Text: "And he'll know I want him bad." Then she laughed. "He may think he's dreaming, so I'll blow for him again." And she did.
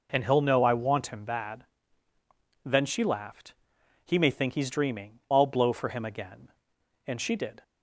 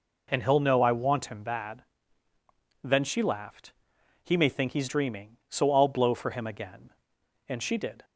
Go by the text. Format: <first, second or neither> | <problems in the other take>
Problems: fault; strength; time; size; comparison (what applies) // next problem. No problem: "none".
second | skips "so"; at 5.2 s